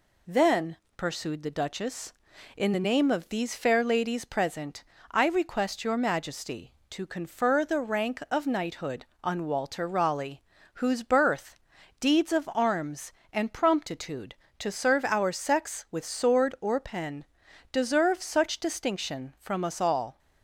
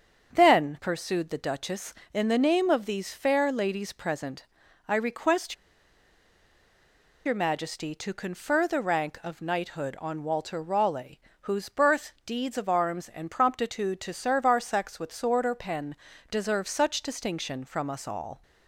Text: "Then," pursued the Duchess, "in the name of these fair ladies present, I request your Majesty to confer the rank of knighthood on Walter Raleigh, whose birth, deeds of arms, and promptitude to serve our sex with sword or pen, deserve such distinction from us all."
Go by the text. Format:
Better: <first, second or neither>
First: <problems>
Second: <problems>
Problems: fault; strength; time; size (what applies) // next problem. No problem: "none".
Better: first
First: none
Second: starts louder than the rest; strong; until 1.3 s; 7 dB // pauses between "request" and "your"; strong; at 5.5 s; 1.7 s long